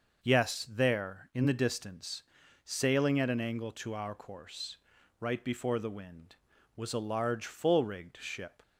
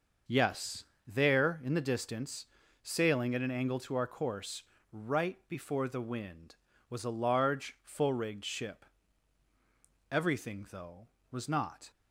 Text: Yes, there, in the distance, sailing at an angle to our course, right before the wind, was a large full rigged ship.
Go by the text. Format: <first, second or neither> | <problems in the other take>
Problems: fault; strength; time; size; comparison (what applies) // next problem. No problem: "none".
first | starts louder than the rest; until 1.4 s; 6.5 dB // goes on to say "Everything though was not"; from 10.3 s on; 1.5 s long